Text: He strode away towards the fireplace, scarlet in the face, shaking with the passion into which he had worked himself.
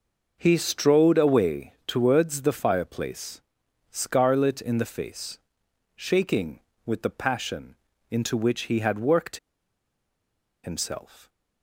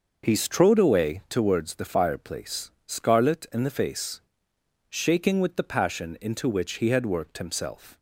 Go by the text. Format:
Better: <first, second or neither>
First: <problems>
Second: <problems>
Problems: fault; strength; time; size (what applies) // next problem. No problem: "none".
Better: second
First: pauses between "away" and "towards"; slight; at 1.7 s; 0.16 s long // pauses between "passion" and "into"; slight; at 7.7 s; 0.34 s long // pauses between "worked" and "himself"; strong; at 9.3 s; 1.2 s long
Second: none